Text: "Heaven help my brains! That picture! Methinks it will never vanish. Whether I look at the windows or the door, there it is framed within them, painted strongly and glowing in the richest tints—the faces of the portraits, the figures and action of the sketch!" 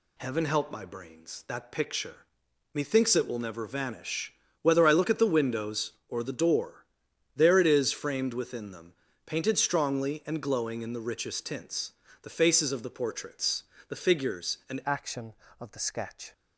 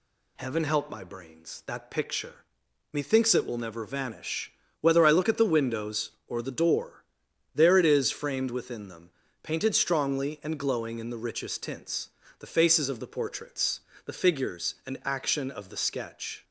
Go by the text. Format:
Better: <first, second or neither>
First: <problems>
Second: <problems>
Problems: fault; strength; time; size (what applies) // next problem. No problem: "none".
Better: second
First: changes voice at "action"; from 14.8 s on; 1.5 s long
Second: none